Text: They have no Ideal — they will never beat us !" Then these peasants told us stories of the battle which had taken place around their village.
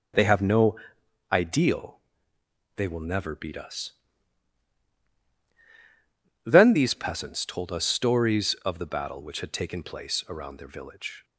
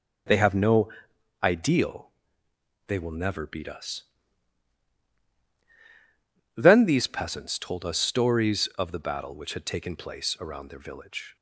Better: neither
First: pauses between "no" and "Ideal"; noticeable; at 0.7 s; 0.56 s long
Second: pauses between "no" and "Ideal"; noticeable; at 0.8 s; 0.54 s long

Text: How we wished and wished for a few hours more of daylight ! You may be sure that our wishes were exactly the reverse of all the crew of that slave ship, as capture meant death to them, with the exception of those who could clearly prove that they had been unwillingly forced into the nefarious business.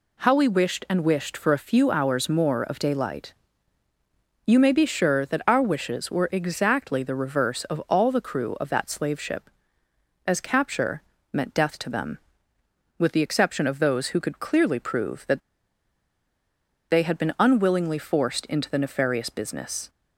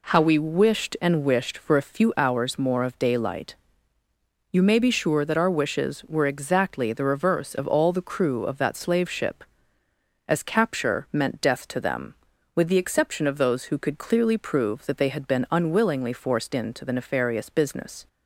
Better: second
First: pauses between "capture" and "meant"; slight; at 11.0 s; 0.28 s long // pauses between "that" and "they"; strong; at 15.3 s; 1.5 s long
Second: none

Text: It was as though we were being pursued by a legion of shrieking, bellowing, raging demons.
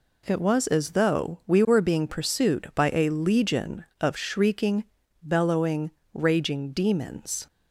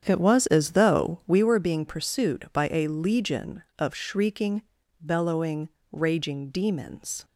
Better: first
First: none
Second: starts louder than the rest; strong; until 1.4 s; 8.5 dB

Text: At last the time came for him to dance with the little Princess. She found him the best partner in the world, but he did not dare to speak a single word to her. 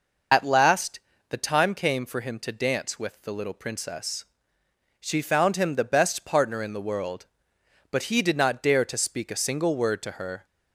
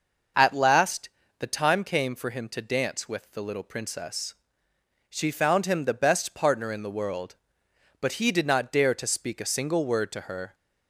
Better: second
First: loses the start of "At"; at 0.3 s; 45 ms // pauses between "last" and "the"; slight; at 0.9 s; 0.30 s long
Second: pauses between "last" and "the"; slight; at 1.0 s; 0.30 s long

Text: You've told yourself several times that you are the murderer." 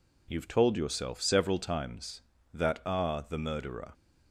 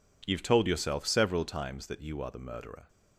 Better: second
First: skips "you"; at 2.8 s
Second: none

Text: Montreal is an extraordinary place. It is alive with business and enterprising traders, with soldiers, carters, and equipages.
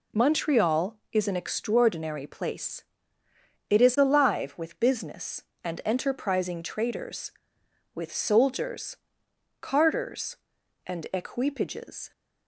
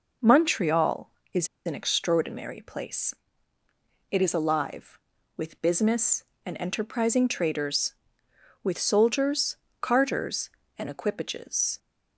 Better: first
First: none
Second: pauses between "is" and "an"; slight; at 1.4 s; 0.18 s long

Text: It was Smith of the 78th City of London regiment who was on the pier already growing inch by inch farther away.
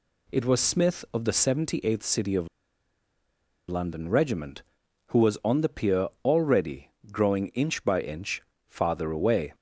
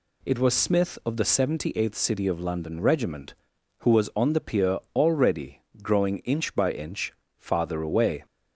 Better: second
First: pauses between "of" and "London"; at 2.4 s; 1.2 s long // pauses between "already" and "growing"; slight; at 6.9 s; 0.20 s long // pauses between "inch" and "farther"; slight; at 8.4 s; 0.24 s long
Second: pauses between "already" and "growing"; slight; at 5.6 s; 0.20 s long // pauses between "inch" and "farther"; slight; at 7.1 s; 0.24 s long

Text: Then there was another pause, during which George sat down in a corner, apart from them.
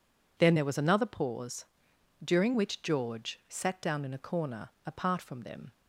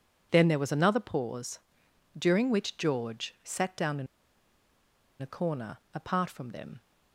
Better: first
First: none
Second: pauses between "in" and "a"; at 4.0 s; 1.1 s long

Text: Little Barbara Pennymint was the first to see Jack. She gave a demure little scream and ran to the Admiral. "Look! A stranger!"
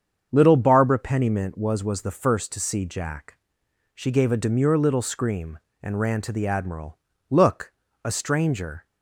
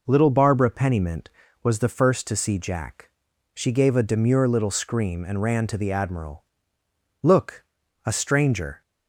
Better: second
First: starts louder than the rest; strong; until 1.3 s; 7.5 dB // says "was" twice; at 1.8 s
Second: none

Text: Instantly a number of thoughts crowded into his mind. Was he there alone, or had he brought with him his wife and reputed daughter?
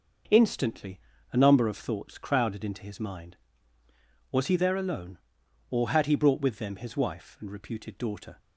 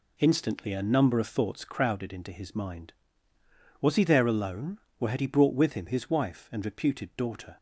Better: second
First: pauses between "Instantly" and "a"; slight; at 0.9 s; 0.34 s long // says "them" for "him"; at 6.5 s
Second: none

